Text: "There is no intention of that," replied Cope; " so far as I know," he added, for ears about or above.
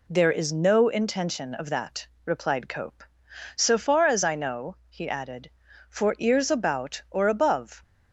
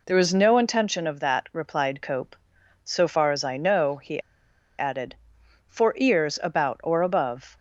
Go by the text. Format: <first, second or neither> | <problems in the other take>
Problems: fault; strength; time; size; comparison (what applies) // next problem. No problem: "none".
first | pauses between "he" and "added"; noticeable; at 4.1 s; 0.58 s long